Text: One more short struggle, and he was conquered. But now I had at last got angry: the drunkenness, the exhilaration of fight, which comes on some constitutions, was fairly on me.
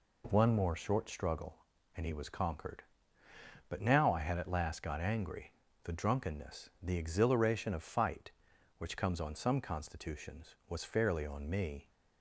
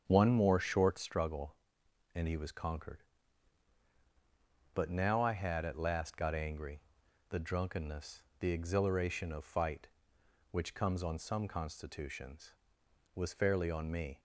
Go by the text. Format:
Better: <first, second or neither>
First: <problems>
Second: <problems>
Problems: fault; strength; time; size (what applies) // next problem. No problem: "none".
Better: first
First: none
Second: starts louder than the rest; strong; until 1.2 s; 7.5 dB